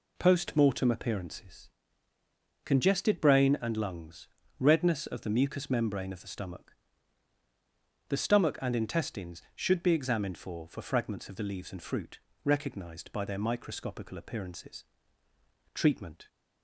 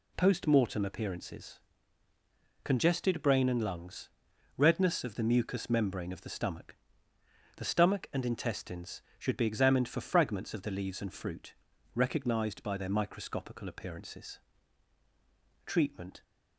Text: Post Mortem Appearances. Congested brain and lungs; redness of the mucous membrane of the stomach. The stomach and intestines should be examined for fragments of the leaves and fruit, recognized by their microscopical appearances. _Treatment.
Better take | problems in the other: second | says "for" twice; at 10.6 s

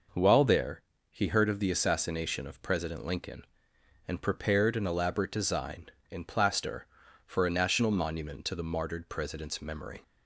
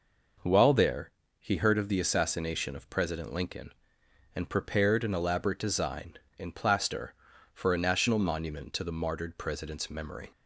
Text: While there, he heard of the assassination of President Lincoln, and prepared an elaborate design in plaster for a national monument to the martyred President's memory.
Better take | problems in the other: neither | none

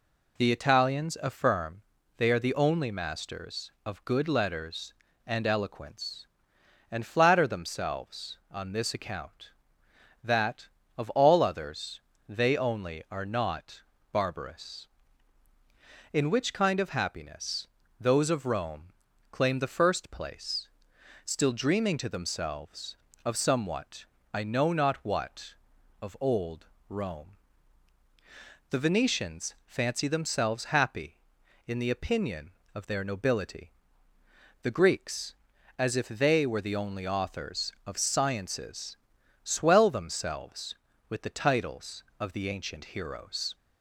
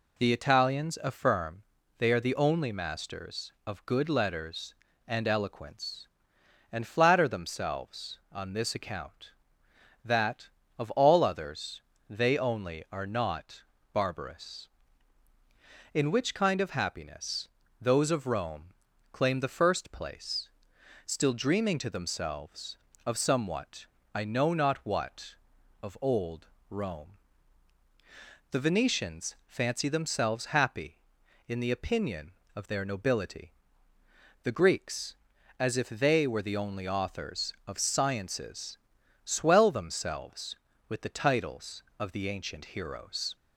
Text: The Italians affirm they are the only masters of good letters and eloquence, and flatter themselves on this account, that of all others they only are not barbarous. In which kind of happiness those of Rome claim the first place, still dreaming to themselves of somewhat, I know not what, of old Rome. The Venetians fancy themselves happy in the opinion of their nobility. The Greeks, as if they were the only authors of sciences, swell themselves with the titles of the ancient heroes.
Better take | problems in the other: neither | pauses between "affirm" and "they"; slight; the same in both // pauses between "others" and "they"; slight; the same in both // pauses between "not" and "barbarous"; slight; the same in both // pauses between "happiness" and "those"; slight; the same in both // pauses between "Rome" and "claim"; the same in both // pauses between "old" and "Rome"; slight; the same in both

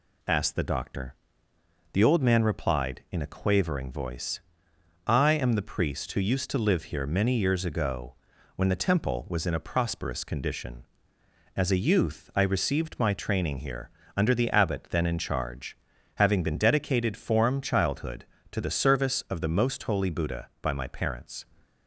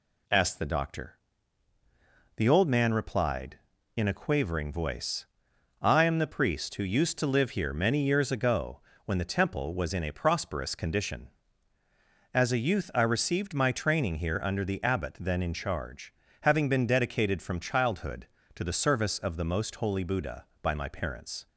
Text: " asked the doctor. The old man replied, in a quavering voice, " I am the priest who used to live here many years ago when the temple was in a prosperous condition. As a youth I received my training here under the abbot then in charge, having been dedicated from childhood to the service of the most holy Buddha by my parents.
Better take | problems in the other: second | pauses between "ago" and "when"; at 8.1 s; 0.40 s long; slight in the second // pauses between "here" and "under"; slight; at 13.8 s; 0.26 s long // says "form" for "from"; at 17.1 s

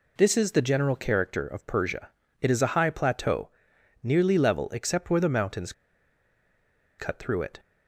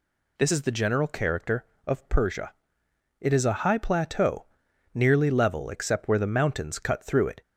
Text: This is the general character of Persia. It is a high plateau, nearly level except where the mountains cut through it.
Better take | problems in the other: second | pauses between "mountains" and "cut"; strong; at 5.7 s; 1.2 s long

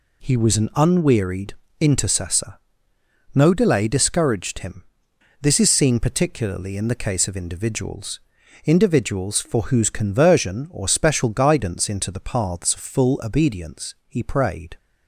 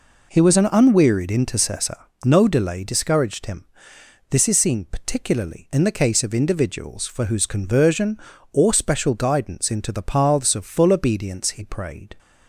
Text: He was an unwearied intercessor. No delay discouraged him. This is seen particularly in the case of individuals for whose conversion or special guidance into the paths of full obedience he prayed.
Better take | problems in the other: second | pauses between "unwearied" and "intercessor"; slight; at 1.5 s; 0.24 s long // says "individuals" twice; at 8.6 s

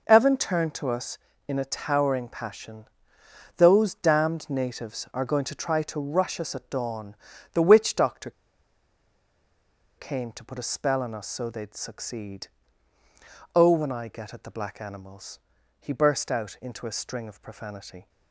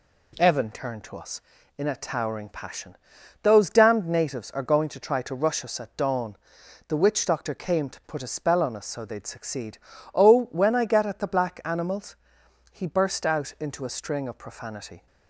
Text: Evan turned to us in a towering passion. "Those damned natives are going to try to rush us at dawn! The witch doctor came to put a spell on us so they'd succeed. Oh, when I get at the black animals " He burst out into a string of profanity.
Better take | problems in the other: second | pauses between "doctor" and "came"; strong; at 8.2 s; 1.6 s long

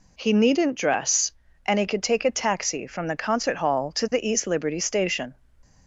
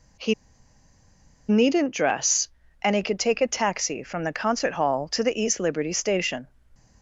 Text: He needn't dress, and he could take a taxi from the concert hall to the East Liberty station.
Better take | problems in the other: first | pauses between "He" and "needn't"; at 0.3 s; 1.1 s long

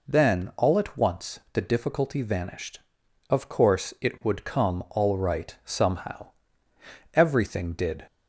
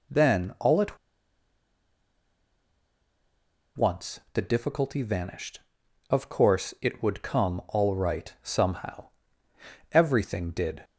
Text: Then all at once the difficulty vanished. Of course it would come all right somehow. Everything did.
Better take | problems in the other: first | pauses between "at" and "once"; strong; at 0.9 s; 2.8 s long

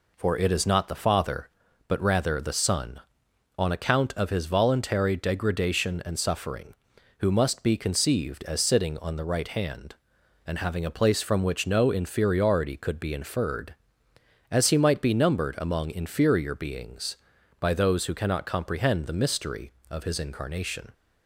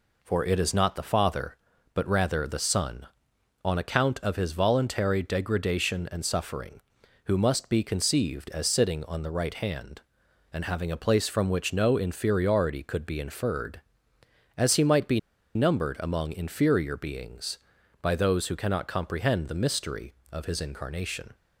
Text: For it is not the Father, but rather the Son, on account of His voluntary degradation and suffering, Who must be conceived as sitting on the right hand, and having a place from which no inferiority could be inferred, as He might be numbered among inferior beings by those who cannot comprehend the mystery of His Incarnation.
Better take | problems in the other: first | pauses between "be" and "numbered"; slight; at 15.1 s; 0.36 s long

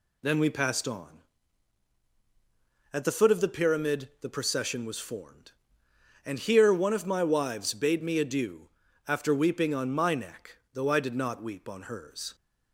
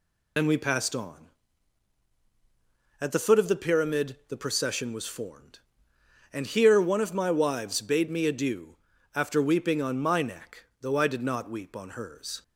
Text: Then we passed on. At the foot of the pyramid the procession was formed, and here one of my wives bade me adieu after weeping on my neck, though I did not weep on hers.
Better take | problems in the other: first | loses the start of "Then"; at 0.3 s; 80 ms // pauses between "adieu" and "after"; at 8.7 s; 0.38 s long; also in the first

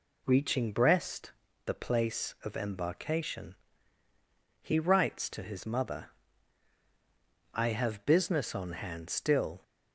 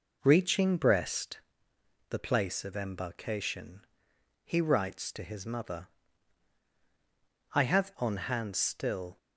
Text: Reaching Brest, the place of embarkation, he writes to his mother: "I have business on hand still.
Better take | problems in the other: first | skips "business"; at 7.9 s

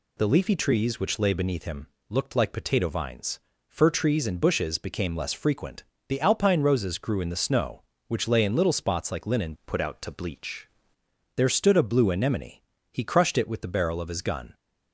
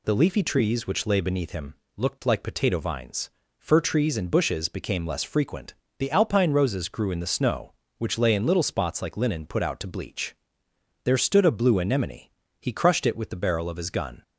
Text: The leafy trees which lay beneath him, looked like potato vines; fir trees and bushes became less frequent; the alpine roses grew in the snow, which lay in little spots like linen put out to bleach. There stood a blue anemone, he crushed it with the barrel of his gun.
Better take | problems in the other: second | changes voice from "put" to "bleach"; from 9.6 to 10.6 s; 1.0 s long

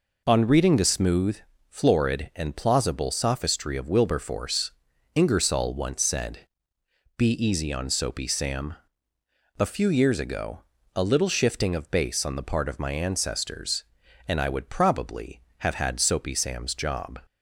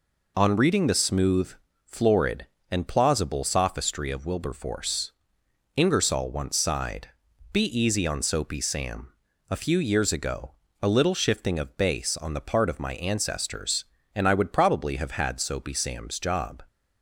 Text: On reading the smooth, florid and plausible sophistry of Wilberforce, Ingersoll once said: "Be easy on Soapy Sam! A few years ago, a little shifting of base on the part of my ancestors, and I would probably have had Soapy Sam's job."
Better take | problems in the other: first | says "sighed" for "said"; at 6.5 s

